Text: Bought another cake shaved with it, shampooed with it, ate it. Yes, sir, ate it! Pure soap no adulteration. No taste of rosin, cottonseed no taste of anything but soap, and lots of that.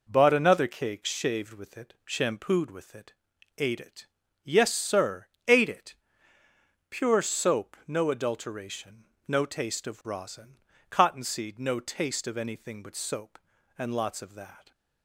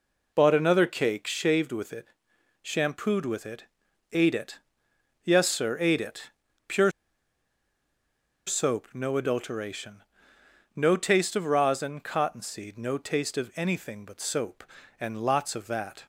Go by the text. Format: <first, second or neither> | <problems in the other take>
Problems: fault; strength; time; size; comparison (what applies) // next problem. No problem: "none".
first | pauses between "Pure" and "soap"; strong; at 6.9 s; 1.5 s long